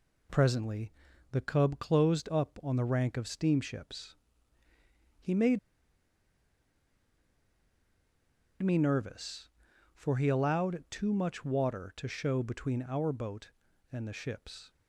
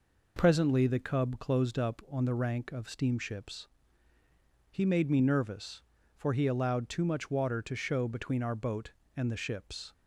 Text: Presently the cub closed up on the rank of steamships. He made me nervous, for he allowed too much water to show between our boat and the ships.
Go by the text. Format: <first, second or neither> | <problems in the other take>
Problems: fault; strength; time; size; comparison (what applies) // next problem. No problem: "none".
second | pauses between "Presently" and "the"; at 0.9 s; 0.40 s long // pauses between "made" and "me"; strong; at 5.5 s; 3.0 s long